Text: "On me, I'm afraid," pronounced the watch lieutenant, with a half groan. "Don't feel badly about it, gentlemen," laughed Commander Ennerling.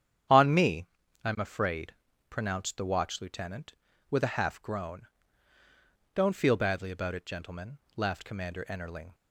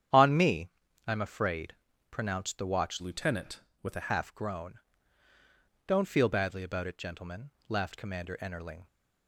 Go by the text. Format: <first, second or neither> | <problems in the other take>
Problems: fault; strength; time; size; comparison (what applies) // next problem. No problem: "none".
first | starts louder than the rest; strong; until 1.5 s; 9 dB; strong in the first // changes voice from "lieutenant" to "a"; from 3.0 to 4.0 s; 1.0 s long